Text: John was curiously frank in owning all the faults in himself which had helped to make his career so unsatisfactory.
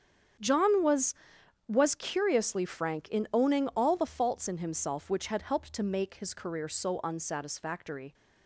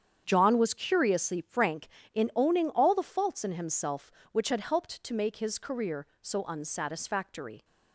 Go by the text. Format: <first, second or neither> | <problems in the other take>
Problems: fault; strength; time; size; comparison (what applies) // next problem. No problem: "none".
second | starts louder than the rest; strong; until 1.9 s; 8 dB; strong in the second // says "was" twice; at 1.6 s